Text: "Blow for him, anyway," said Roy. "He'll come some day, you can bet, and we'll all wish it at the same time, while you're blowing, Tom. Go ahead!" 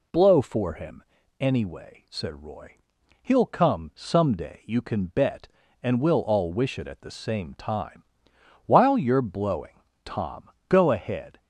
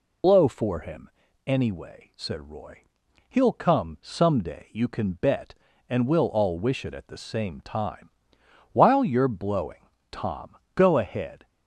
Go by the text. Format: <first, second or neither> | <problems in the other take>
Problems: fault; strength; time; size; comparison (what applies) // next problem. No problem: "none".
first | loses the start of "Blow"; at 0.2 s; 55 ms